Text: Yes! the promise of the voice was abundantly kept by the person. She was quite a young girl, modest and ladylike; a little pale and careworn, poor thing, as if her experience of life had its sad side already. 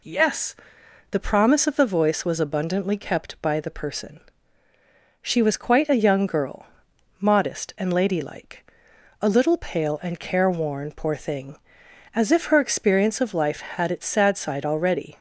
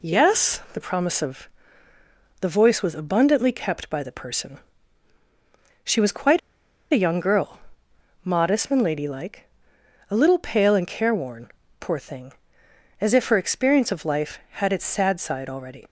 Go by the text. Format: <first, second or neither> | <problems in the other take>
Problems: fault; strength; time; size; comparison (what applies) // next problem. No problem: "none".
first | pauses between "of" and "the"; noticeable; at 1.4 s; 0.92 s long // pauses between "quite" and "a"; noticeable; at 6.3 s; 0.52 s long